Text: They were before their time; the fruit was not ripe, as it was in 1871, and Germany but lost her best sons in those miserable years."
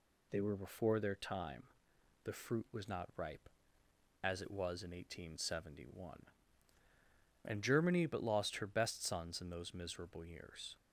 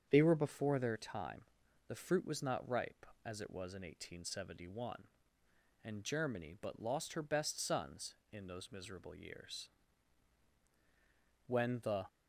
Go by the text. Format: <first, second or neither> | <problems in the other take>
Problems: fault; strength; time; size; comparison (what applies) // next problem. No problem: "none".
first | starts louder than the rest; strong; until 1.0 s; 8 dB // goes on to say "When the"; from 11.4 s on; 0.58 s long